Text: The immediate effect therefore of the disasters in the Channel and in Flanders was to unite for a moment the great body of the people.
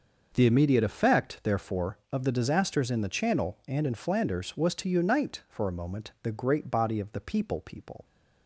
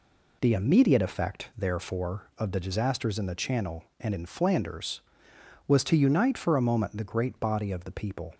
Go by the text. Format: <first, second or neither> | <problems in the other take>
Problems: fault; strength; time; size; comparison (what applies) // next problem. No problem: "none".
second | starts louder than the rest; until 1.3 s; 6 dB // says "people" twice; at 7.6 s